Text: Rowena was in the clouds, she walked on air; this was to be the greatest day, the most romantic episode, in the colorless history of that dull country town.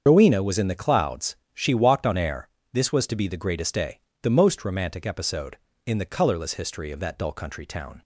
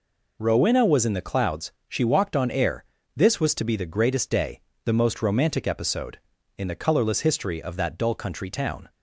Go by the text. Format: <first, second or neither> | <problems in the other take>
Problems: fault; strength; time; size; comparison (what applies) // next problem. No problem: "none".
second | loses the start of "Rowena"; at 0.0 s; 85 ms // starts louder than the rest; until 1.0 s; 7 dB